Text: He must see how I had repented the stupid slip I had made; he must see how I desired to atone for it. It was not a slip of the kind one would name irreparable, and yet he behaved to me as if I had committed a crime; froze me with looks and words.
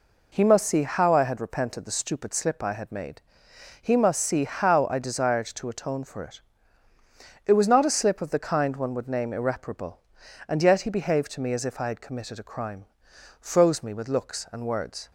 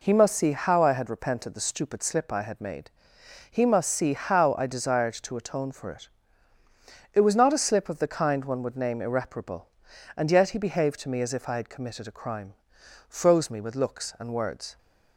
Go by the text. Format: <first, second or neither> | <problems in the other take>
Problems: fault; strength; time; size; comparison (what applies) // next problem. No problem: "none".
neither | none